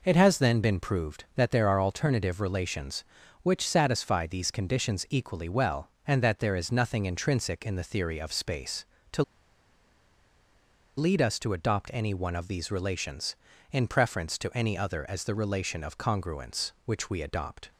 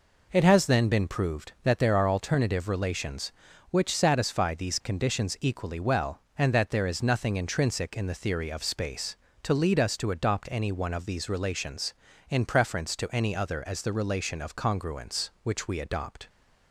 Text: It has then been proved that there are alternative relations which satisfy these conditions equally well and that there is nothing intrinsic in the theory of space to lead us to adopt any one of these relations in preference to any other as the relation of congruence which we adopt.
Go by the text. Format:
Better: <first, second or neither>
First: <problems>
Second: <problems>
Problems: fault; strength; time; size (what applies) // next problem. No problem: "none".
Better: second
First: pauses between "to" and "lead"; strong; at 9.2 s; 1.7 s long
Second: none